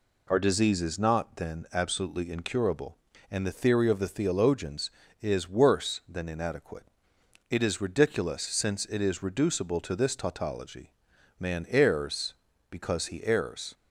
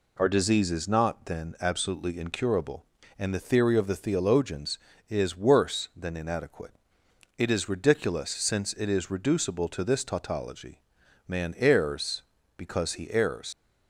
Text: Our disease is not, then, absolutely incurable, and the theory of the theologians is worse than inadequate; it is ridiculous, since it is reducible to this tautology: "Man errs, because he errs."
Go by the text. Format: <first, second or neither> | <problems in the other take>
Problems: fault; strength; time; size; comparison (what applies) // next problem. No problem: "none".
first | leaves "errs" unfinished; at 13.5 s; 75 ms